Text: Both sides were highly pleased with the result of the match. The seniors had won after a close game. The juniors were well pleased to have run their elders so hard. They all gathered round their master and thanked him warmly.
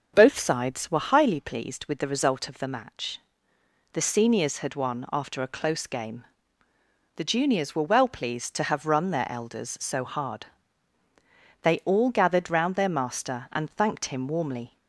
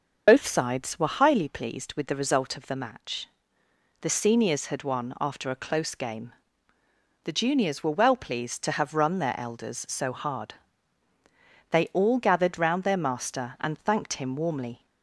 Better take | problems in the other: first | loses the start of "Both"; at 0.2 s; 50 ms // starts louder than the rest; noticeable; until 1.2 s; 6 dB; noticeable in the first

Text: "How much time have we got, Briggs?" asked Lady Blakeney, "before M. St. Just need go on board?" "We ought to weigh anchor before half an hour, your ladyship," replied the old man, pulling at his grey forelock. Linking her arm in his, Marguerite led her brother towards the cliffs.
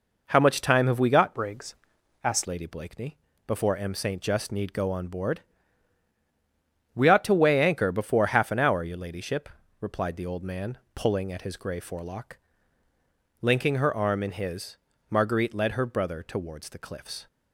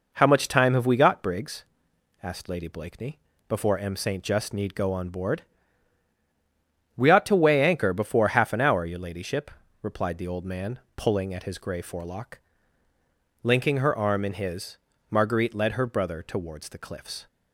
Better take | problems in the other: second | changes voice from "Briggs" to "asked"; from 1.3 to 2.4 s; 1.1 s long

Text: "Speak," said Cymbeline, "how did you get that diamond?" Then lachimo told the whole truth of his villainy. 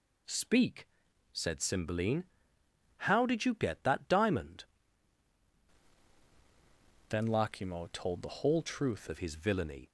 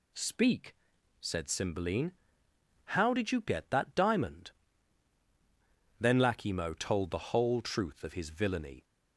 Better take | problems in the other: second | changes voice from "Then" to "truth"; from 7.0 to 9.0 s; 2.0 s long

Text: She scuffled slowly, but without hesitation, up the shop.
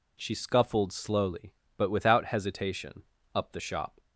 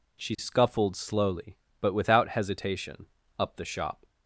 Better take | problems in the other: neither | none

